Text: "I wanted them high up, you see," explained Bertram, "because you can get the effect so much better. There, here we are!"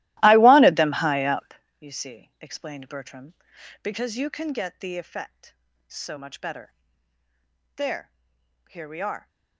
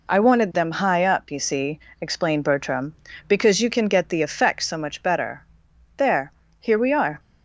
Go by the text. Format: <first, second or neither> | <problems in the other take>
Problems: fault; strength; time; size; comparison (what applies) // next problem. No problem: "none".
second | starts louder than the rest; strong; until 1.6 s; 16.5 dB